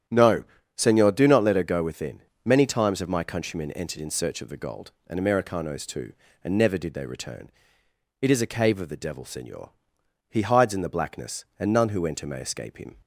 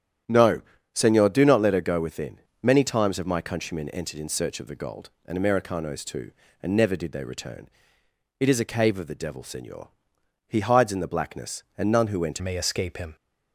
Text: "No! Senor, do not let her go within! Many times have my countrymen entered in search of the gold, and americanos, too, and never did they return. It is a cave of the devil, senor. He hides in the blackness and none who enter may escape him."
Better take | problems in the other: first | starts louder than the rest; strong; until 1.5 s; 10 dB; strong in the first // changes voice at "may"; from 12.3 s on; 0.8 s long

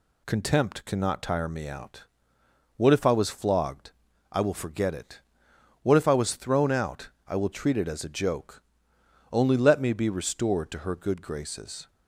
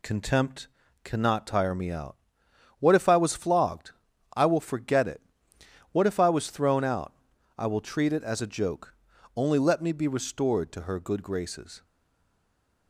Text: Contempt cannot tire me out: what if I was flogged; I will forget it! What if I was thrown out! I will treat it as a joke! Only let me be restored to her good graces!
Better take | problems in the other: first | pauses between "Contempt" and "cannot"; slight; at 0.6 s; 0.36 s long // stays silent after the last word; from 11.8 s on; 1.0 s long

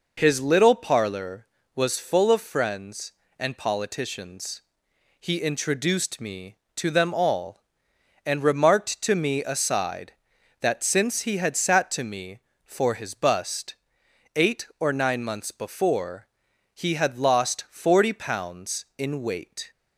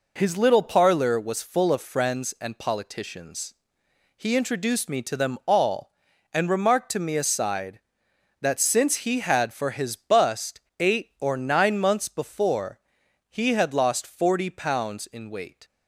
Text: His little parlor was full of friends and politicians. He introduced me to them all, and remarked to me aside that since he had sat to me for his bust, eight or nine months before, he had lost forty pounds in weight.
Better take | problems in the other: first | skips "sat to me"; at 9.5 s

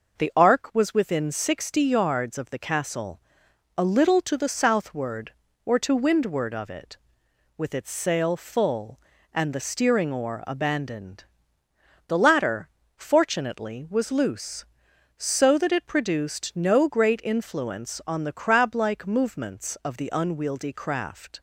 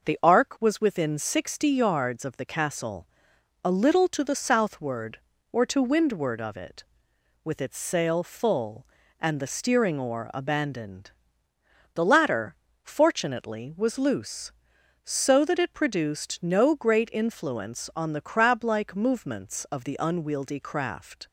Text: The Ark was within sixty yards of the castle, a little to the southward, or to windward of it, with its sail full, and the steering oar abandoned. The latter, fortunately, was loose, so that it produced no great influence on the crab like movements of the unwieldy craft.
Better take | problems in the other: neither | none

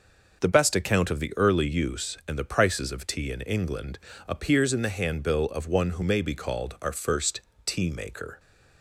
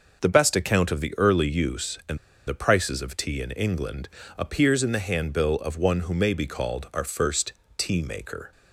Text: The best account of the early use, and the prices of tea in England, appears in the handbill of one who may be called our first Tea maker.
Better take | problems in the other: first | pauses between "and" and "the"; slight; at 2.1 s; 0.29 s long // pauses between "first" and "Tea"; slight; at 7.5 s; 0.24 s long; slight in the first

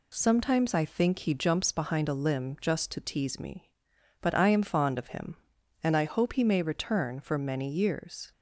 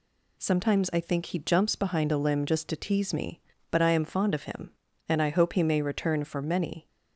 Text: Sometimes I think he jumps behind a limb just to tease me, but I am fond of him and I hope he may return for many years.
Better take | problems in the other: first | stops before "years"; at 6.8 s

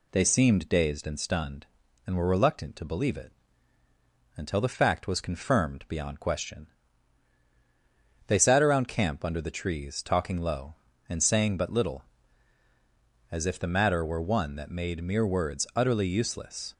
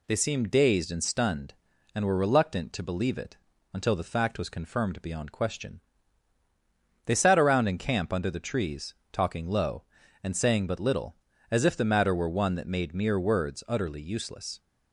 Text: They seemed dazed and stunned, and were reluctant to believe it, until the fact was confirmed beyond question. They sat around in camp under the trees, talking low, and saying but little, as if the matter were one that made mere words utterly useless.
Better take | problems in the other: second | skips "in"; at 8.8 s

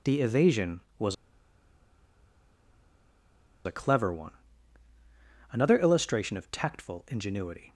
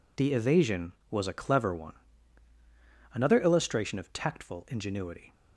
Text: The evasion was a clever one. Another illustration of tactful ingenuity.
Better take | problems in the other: second | pauses between "was" and "a"; strong; at 1.1 s; 2.5 s long

